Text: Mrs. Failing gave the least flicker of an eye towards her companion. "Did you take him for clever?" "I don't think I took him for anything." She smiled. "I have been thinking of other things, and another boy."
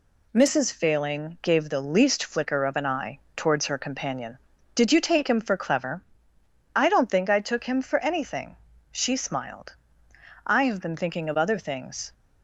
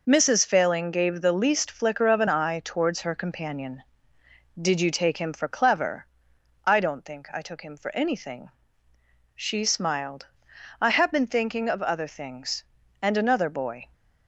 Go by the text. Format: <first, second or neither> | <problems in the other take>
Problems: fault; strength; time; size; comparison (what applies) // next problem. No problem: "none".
second | pauses between "eye" and "towards"; slight; at 3.1 s; 0.18 s long // stops before "and another boy"; at 12.1 s